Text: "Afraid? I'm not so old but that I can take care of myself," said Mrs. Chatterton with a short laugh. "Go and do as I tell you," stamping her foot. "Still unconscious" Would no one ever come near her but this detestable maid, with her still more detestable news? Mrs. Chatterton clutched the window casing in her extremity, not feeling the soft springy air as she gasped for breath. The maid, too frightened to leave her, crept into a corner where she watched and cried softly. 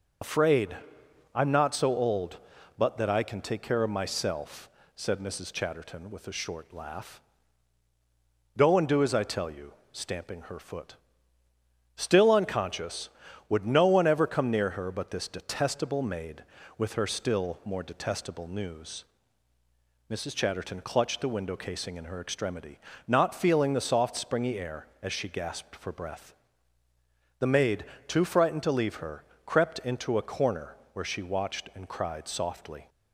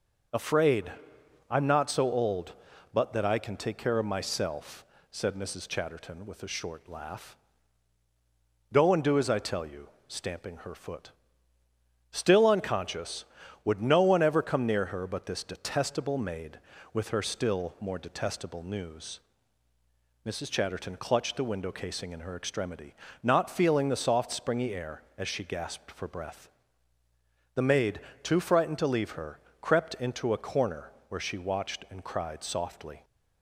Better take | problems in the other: second | loses the start of "Afraid"; at 0.2 s; 50 ms // starts louder than the rest; noticeable; until 1.8 s; 6 dB // pauses between "corner" and "where"; slight; at 30.7 s; 0.20 s long; slight in the second

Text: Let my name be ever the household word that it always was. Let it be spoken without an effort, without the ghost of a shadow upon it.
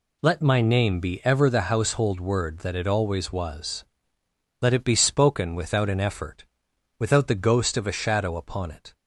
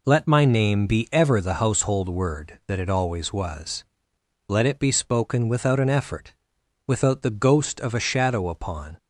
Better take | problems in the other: first | stops before "it"; at 8.9 s

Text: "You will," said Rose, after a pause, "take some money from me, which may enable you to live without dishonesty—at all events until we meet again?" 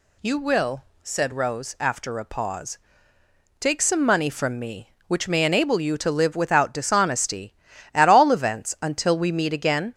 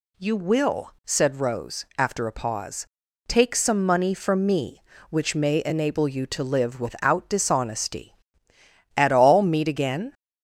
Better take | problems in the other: first | skips "events until we"; at 9.4 s

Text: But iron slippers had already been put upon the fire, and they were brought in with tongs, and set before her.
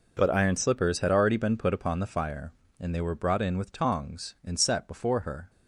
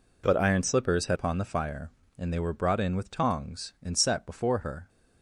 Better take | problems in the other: first | skips "already been put"; at 1.1 s

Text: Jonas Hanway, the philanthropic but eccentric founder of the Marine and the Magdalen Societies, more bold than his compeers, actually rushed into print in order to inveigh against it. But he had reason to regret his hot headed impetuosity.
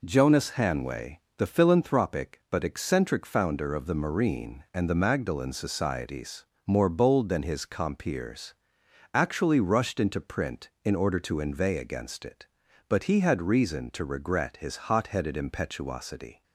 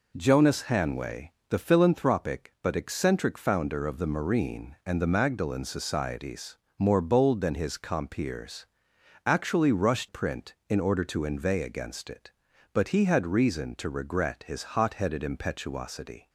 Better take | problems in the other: first | skips "into"; at 10.0 s

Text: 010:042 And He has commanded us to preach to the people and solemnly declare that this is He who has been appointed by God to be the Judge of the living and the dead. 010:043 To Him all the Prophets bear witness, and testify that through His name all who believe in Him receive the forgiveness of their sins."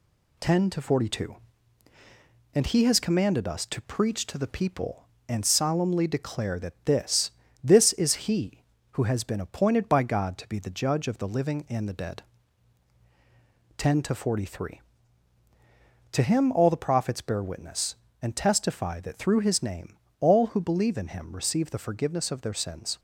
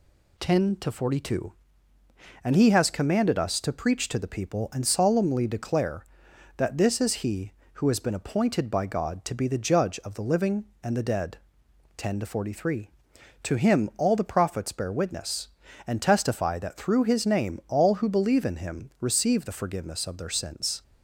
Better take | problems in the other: second | says "this" twice; at 7.6 s // pauses between "name" and "all"; slight; at 19.9 s; 0.22 s long

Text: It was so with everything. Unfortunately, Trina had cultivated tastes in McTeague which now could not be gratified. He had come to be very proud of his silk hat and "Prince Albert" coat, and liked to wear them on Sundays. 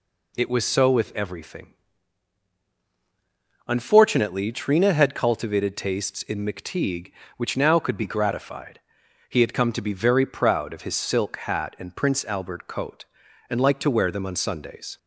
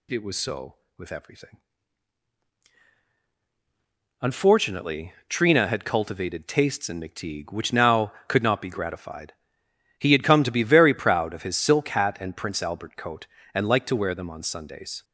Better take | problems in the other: second | skips "not"; at 7.9 s

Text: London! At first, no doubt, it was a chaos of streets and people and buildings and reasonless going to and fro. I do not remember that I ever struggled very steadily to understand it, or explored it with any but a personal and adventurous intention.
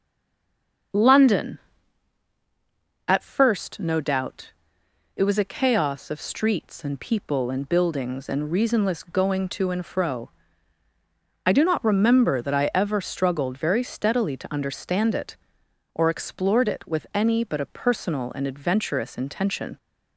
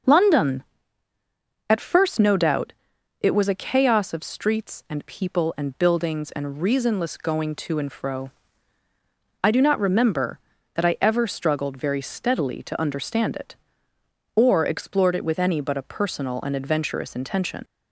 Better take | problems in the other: second | stays silent before the first word; slight; until 0.9 s; 0.9 s long // starts louder than the rest; until 3.4 s; 6.5 dB; noticeable in the second

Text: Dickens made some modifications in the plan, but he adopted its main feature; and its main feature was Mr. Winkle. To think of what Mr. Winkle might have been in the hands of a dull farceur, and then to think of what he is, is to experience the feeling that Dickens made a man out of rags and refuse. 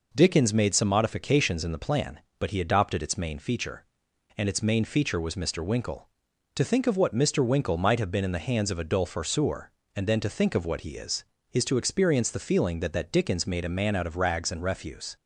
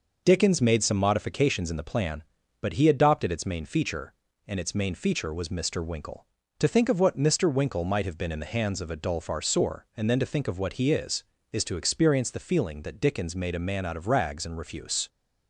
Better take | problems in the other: second | says "that" twice; at 12.9 s

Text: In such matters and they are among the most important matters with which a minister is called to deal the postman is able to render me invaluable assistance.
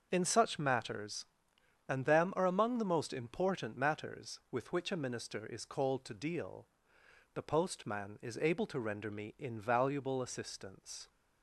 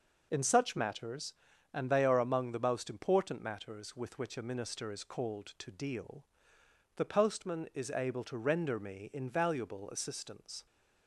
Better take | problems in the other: second | starts louder than the rest; until 1.1 s; 6.5 dB // says "them" for "they"; at 2.0 s // pauses between "deal" and "the"; noticeable; at 6.6 s; 0.68 s long; noticeable in the second

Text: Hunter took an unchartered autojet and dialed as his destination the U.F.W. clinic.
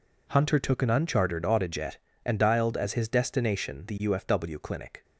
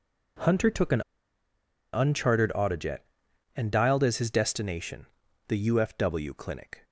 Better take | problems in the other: first | pauses between "an" and "unchartered"; noticeable; at 1.0 s; 0.91 s long // pauses between "destination" and "the"; at 5.0 s; 0.42 s long

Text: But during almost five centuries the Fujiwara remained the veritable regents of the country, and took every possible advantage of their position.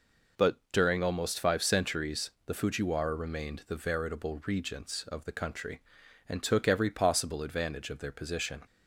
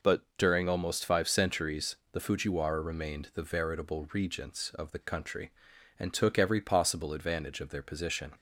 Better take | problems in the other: neither | pauses between "But" and "during"; slight; the same in both // pauses between "centuries" and "the"; slight; the same in both

